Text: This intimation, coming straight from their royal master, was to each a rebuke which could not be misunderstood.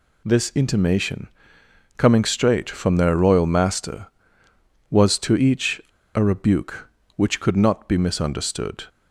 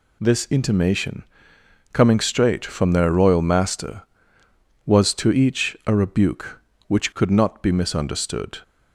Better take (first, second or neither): second